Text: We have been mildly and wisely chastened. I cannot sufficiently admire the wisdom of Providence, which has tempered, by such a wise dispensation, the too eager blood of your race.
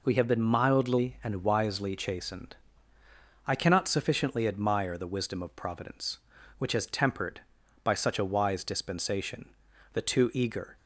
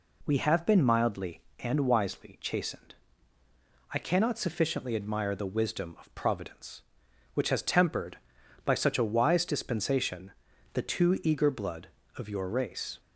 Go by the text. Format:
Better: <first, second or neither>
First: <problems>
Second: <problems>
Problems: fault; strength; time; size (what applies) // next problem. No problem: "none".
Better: second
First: stops before "blood of your race"; at 10.7 s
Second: none